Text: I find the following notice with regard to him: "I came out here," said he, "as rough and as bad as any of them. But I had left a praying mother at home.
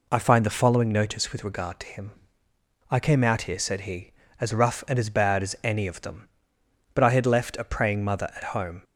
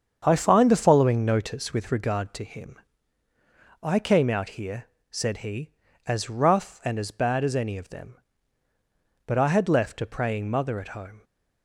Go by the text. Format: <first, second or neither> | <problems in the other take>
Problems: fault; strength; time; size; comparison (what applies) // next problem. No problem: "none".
first | starts louder than the rest; strong; until 2.0 s; 7.5 dB